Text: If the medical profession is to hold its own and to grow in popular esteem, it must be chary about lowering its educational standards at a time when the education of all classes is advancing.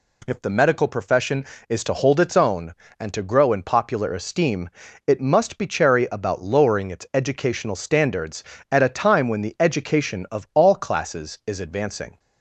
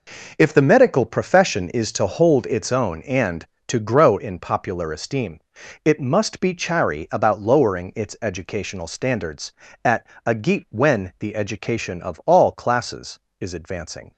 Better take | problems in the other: first | pauses between "at" and "a"; slight; at 10.0 s; 0.18 s long // says "geet" for "time"; at 10.3 s

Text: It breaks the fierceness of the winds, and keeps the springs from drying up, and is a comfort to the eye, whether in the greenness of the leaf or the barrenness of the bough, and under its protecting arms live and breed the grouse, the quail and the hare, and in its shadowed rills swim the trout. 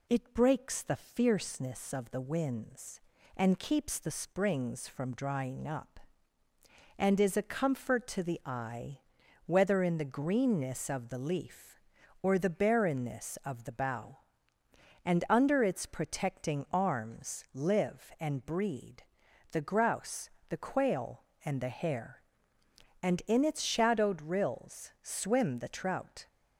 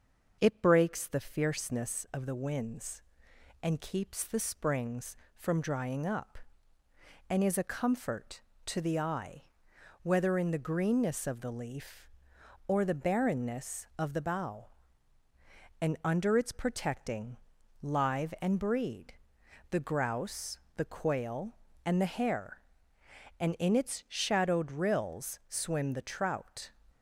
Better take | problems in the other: first | starts louder than the rest; noticeable; until 1.4 s; 6 dB // skips "arms"; at 17.5 s // pauses between "breed" and "the"; noticeable; at 19.1 s; 0.56 s long; noticeable in the first

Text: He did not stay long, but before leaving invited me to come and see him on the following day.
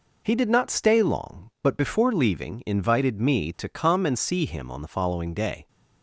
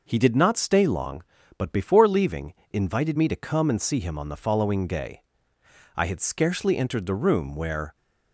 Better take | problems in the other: first | pauses between "leaving" and "invited"; slight; at 2.5 s; 0.18 s long // goes on to say "I had scarcely entered the room where"; strong; from 5.9 s on; 2.0 s long

